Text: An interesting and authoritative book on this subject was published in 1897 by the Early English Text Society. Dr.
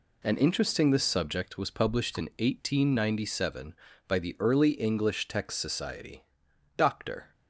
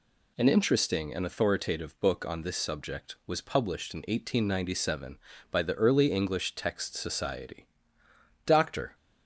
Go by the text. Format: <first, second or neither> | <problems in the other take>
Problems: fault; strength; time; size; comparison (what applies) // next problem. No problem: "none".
second | skips "and authoritative book on"; at 0.9 s